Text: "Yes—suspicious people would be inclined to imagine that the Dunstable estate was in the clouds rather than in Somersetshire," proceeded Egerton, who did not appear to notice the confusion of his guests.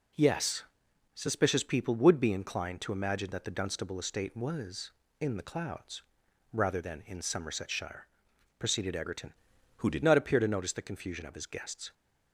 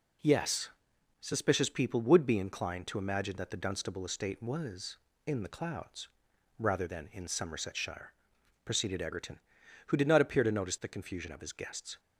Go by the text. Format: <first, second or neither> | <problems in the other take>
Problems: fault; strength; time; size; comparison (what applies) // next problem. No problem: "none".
second | pauses between "clouds" and "rather"; noticeable; at 6.0 s; 0.48 s long; noticeable in the second // changes voice from "who" to "did"; from 9.7 to 10.0 s; 0.3 s long